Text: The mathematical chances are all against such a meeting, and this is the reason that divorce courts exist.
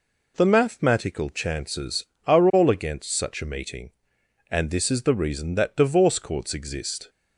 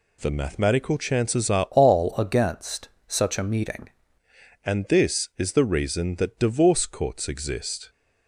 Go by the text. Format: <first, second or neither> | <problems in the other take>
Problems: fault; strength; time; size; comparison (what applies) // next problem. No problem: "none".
first | changes voice from "all" to "meeting"; from 1.7 to 3.8 s; 2.1 s long // pauses between "against" and "such"; slight; at 2.8 s; 0.18 s long